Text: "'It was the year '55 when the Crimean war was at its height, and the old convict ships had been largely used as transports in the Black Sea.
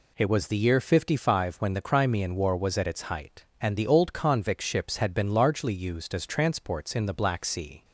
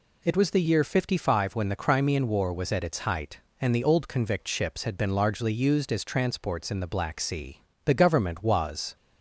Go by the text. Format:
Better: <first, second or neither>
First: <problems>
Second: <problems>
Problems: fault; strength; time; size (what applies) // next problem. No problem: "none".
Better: first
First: none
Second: goes on to say "The government was"; noticeable; from 7.8 s on; 1.1 s long